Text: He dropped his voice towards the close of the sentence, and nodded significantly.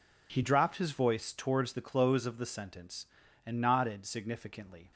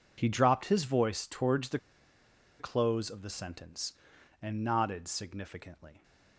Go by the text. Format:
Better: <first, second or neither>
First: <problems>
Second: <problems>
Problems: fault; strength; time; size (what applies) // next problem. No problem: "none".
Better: first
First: none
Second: pauses between "the" and "close"; noticeable; at 1.7 s; 0.80 s long